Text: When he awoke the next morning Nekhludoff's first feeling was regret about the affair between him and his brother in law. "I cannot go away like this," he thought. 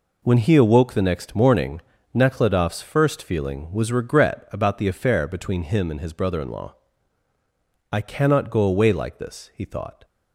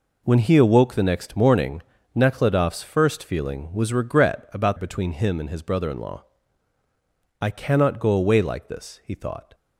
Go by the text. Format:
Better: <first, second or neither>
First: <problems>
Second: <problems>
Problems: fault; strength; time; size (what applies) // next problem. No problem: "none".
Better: first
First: pauses between "morning" and "Nekhludoff's"; slight; at 1.8 s; 0.32 s long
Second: pauses between "morning" and "Nekhludoff's"; slight; at 1.8 s; 0.32 s long // skips "the affair"; at 4.7 s